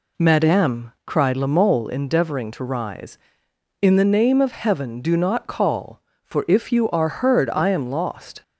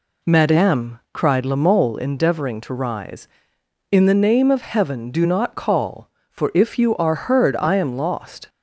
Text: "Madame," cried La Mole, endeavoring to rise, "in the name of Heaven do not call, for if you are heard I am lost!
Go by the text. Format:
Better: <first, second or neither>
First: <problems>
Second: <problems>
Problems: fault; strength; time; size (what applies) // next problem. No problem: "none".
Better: neither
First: none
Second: none